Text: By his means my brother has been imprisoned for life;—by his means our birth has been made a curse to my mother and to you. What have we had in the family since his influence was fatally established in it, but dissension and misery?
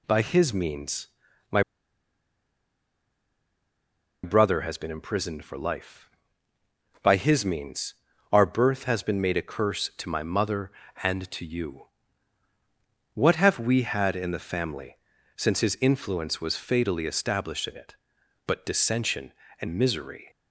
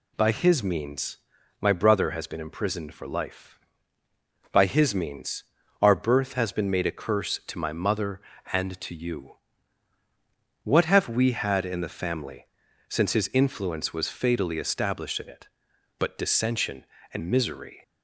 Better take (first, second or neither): second